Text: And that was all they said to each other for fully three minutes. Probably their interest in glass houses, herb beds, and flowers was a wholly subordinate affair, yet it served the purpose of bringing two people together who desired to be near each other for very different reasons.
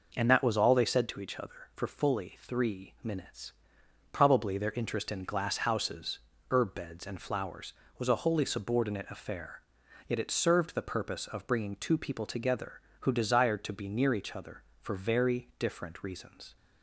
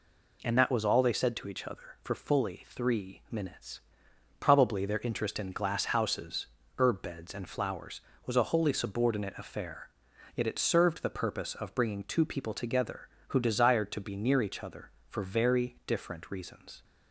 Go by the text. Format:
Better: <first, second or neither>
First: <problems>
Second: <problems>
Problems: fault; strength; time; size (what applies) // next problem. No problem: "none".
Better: second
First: starts louder than the rest; noticeable; until 1.1 s; 5.5 dB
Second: none